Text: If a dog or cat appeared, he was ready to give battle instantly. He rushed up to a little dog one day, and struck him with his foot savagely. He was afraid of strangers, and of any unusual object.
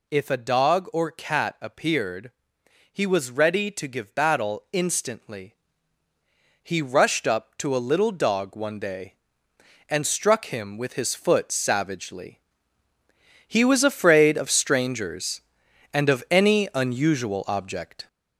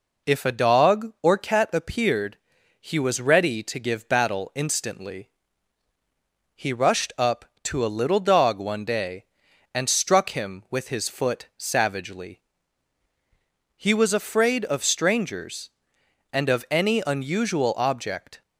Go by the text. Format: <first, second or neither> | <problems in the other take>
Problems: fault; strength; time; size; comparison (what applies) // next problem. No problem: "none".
second | gets louder; noticeable; throughout; 5 dB